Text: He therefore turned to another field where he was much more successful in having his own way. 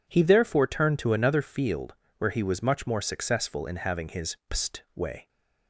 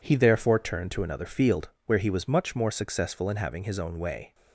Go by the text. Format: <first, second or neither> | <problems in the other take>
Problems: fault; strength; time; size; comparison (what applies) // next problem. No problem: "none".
second | pauses between "field" and "where"; slight; at 1.9 s; 0.24 s long; slight in the second // says "pst" for "own"; at 4.4 s